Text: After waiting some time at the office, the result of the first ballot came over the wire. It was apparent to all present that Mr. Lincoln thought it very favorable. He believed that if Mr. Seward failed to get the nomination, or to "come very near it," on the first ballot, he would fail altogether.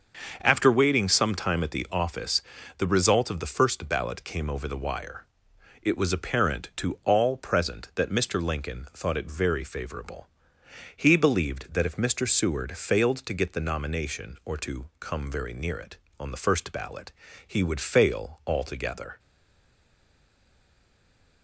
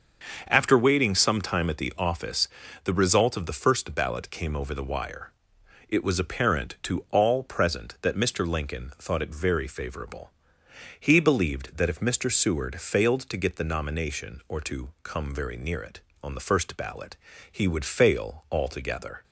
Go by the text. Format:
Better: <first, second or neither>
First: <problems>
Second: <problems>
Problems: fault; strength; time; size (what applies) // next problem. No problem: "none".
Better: second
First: starts louder than the rest; until 1.4 s; 6.5 dB // stays silent after the last word; from 19.1 s on; 2.3 s long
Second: starts louder than the rest; until 1.4 s; 6.5 dB